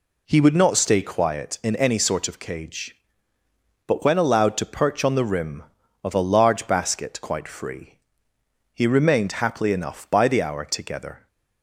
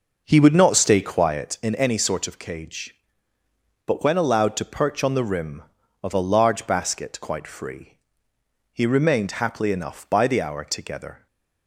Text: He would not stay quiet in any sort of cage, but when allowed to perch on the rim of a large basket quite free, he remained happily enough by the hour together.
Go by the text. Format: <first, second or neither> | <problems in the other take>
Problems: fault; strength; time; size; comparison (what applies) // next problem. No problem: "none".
first | starts louder than the rest; noticeable; until 1.7 s; 5.5 dB // stays silent after the last word; slight; from 11.1 s on; 0.5 s long